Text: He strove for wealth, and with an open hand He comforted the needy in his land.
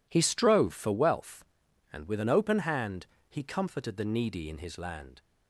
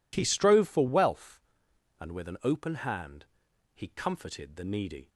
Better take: first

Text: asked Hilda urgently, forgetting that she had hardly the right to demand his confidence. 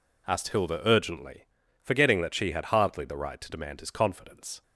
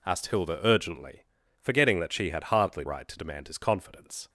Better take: first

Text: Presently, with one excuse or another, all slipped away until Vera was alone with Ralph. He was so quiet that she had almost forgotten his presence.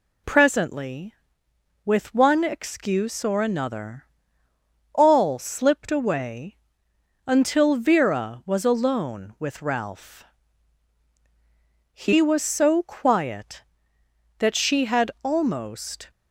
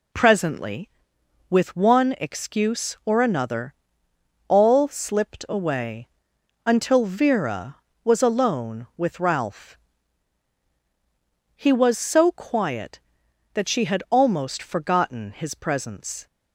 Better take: second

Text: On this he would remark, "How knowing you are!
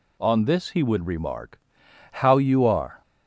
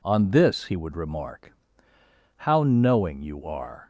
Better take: second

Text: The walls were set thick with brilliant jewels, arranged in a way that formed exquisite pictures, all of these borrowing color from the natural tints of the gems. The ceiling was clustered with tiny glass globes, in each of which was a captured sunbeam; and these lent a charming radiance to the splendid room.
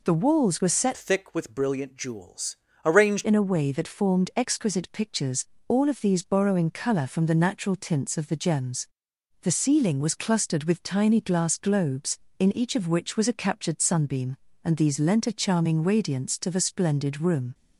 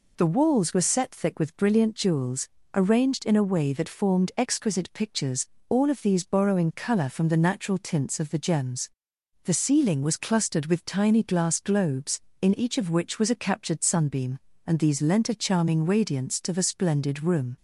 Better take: second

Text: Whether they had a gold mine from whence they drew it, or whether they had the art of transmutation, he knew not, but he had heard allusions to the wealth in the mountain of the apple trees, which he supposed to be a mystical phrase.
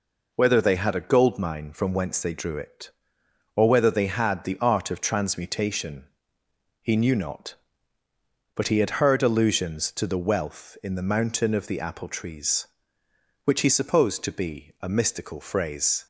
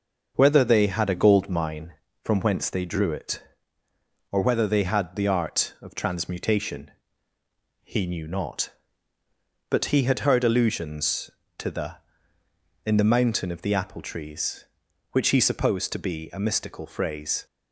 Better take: first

